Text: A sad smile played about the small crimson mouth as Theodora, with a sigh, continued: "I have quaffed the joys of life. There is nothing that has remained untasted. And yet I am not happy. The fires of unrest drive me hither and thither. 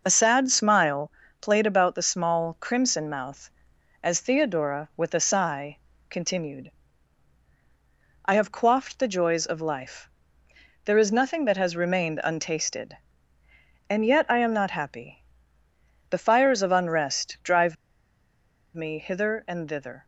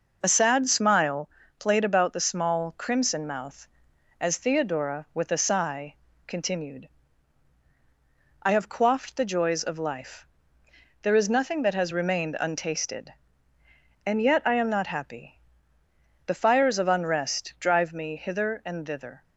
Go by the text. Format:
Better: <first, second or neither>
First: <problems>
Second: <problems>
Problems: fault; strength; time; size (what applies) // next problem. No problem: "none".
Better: second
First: pauses between "smile" and "played"; slight; at 1.1 s; 0.28 s long // pauses between "drive" and "me"; at 17.7 s; 1.0 s long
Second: pauses between "smile" and "played"; slight; at 1.3 s; 0.28 s long